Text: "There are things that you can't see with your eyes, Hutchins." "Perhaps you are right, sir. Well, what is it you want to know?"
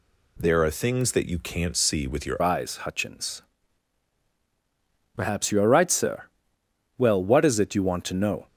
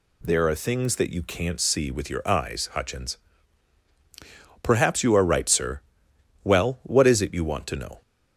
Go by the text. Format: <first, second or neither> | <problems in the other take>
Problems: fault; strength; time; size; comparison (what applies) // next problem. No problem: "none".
second | changes voice at "eyes"; from 2.4 s on; 6.0 s long